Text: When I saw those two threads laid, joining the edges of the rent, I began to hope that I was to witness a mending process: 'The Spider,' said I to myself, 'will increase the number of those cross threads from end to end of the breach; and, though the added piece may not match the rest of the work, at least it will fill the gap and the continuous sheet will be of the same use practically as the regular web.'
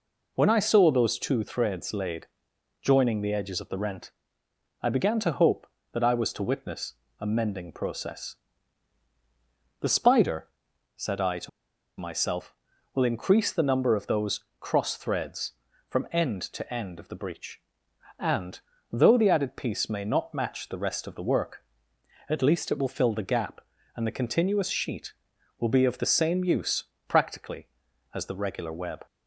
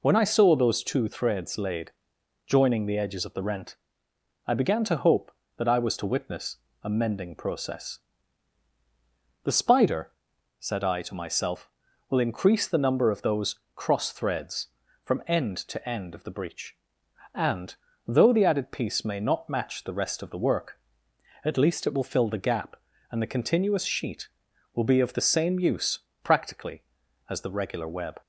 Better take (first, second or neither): second